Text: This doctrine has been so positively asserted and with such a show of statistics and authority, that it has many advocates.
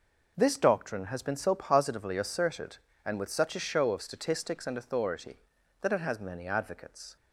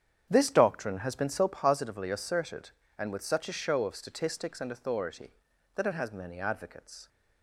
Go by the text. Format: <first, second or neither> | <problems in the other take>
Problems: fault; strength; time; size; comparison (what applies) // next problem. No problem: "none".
first | starts louder than the rest; strong; until 1.6 s; 8.5 dB